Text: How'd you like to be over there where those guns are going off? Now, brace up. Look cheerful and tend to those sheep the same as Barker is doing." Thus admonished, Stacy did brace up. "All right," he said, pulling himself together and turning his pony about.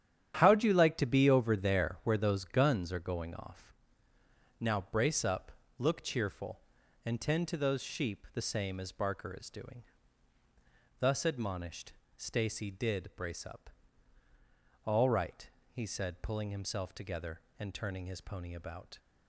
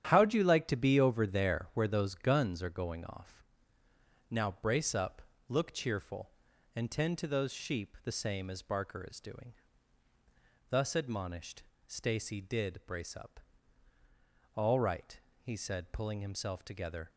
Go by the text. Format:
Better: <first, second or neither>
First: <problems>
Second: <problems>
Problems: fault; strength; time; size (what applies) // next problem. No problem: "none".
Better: first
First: starts louder than the rest; strong; until 1.4 s; 9.5 dB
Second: starts louder than the rest; strong; until 1.1 s; 9.5 dB // stops before "and turning his pony about"; at 17.0 s